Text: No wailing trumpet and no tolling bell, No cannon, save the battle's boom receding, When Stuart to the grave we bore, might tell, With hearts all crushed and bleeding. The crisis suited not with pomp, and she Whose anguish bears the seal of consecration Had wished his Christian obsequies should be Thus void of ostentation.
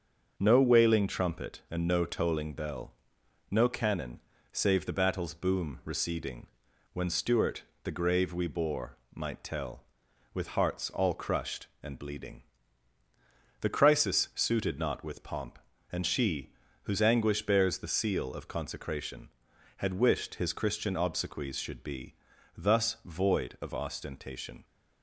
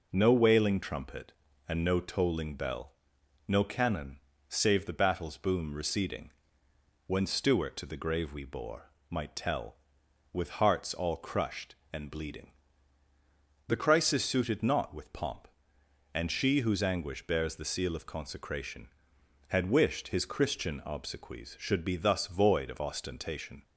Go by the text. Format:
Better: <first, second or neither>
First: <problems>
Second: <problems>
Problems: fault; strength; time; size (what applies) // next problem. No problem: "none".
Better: second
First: starts louder than the rest; until 1.3 s; 6.5 dB // skips "to"; at 7.7 s // pauses between "she" and "Whose"; slight; at 16.5 s; 0.32 s long // pauses between "be" and "Thus"; at 22.1 s; 0.42 s long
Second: none